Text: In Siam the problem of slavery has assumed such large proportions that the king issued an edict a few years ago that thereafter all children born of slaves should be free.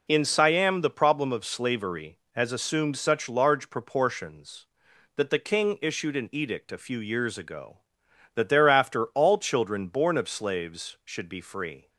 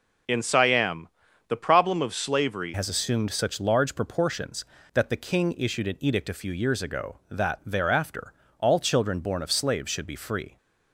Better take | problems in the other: first | pauses between "Siam" and "the"; at 1.0 s; 0.40 s long // changes voice at "has"; from 2.7 s on; 7.8 s long // pauses between "thereafter" and "all"; slight; at 8.3 s; 0.26 s long

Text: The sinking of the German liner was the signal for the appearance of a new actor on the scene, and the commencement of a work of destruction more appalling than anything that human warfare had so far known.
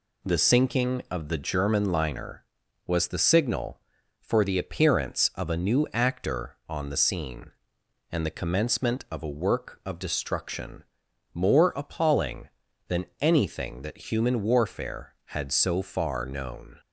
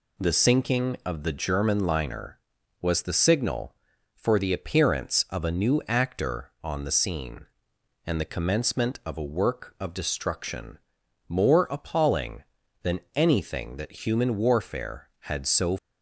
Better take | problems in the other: first | pauses between "destruction" and "more"; noticeable; at 10.7 s; 0.50 s long; noticeable in the first // pauses between "than" and "anything"; slight; at 12.9 s; 0.16 s long; slight in the first // stops before "far known"; at 15.7 s

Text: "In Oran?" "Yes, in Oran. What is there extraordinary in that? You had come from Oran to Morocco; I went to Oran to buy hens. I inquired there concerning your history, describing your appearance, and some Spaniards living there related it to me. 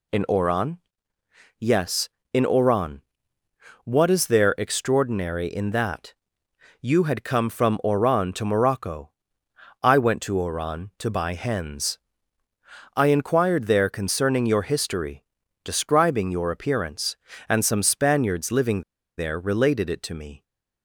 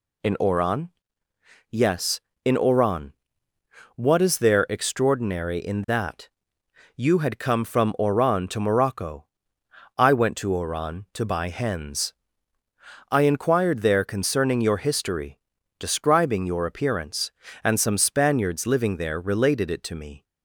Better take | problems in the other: second | pauses between "living" and "there"; at 18.8 s; 0.36 s long

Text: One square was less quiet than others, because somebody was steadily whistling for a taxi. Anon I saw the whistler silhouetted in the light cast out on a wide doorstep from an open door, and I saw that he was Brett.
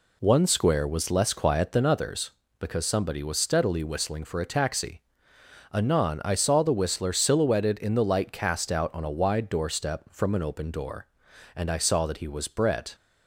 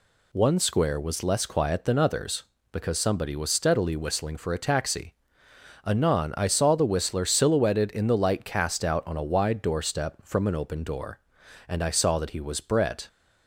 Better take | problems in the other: second | starts louder than the rest; slight; until 1.9 s; 2 dB

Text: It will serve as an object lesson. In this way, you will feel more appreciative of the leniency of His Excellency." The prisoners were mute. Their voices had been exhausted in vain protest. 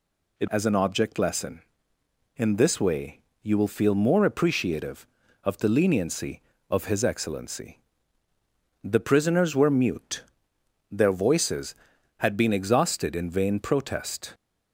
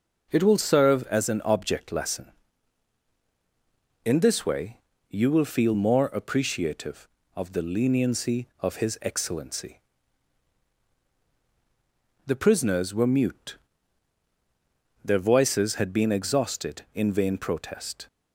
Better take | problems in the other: second | skips "will serve"; at 0.4 s

